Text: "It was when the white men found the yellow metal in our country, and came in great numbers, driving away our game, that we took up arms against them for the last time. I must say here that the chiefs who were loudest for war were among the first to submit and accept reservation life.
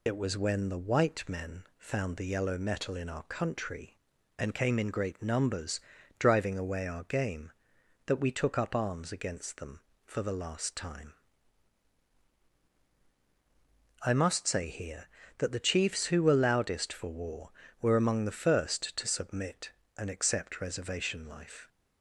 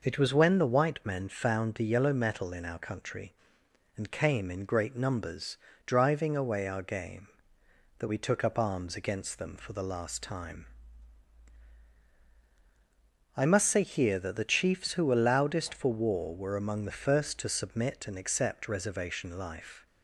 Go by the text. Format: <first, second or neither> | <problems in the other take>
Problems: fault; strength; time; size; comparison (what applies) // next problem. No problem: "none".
second | loses the start of "It"; at 0.0 s; 75 ms